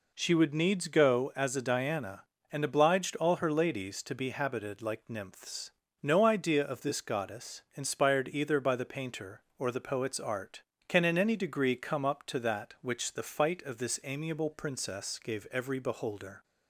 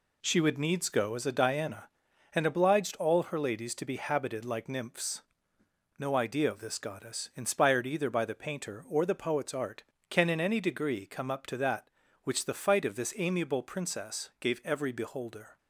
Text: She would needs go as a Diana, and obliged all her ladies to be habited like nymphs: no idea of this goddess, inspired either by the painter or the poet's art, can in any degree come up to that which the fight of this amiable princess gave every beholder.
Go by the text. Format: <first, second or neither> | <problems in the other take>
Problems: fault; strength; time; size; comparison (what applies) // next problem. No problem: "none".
neither | none